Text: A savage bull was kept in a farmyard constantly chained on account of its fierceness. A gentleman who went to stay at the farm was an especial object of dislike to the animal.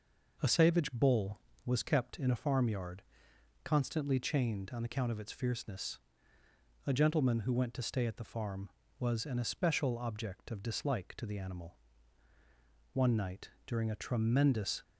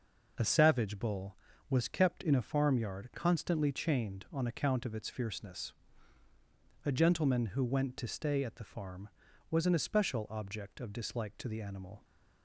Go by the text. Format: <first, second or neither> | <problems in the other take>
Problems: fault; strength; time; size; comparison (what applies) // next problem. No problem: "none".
second | pauses between "farmyard" and "constantly"; noticeable; at 3.0 s; 0.62 s long // goes on to say "One night during a tremendous"; strong; from 12.9 s on; 1.9 s long